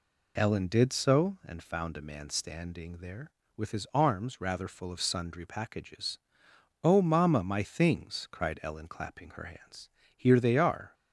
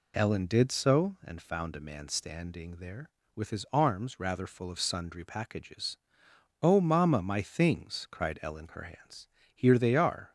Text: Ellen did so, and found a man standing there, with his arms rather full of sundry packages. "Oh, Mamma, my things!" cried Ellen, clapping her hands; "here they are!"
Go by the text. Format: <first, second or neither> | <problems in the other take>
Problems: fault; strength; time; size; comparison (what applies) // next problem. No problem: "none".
first | skips "clapping"; at 8.6 s